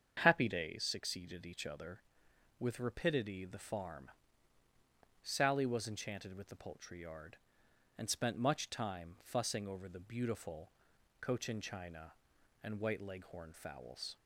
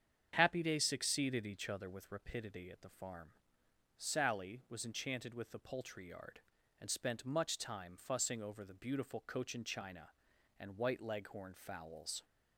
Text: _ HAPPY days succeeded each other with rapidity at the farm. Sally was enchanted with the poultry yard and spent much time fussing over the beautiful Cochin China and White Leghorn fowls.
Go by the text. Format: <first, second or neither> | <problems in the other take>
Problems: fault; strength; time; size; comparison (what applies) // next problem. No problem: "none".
second | starts louder than the rest; strong; until 1.2 s; 7.5 dB; strong in the second // skips "at"; at 3.4 s // pauses between "beautiful" and "Cochin"; noticeable; at 10.7 s; 0.48 s long